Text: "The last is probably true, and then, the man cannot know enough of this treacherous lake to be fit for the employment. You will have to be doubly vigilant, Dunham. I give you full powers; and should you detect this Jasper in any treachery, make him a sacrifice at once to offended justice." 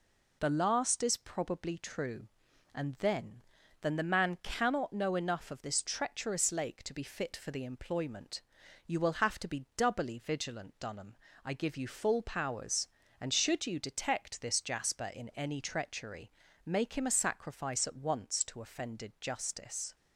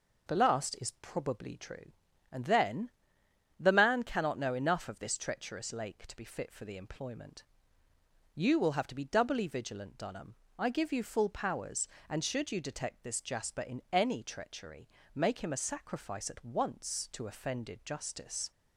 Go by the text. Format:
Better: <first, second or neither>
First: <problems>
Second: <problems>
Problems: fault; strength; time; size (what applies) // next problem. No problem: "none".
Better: second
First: says "then" twice; at 3.8 s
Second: none